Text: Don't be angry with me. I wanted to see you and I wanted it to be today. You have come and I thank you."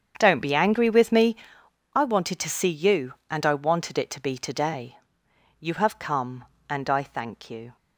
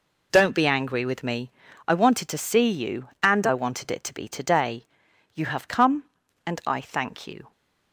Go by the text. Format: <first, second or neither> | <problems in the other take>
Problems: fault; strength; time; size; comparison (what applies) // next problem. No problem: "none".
second | starts louder than the rest; strong; until 1.5 s; 7.5 dB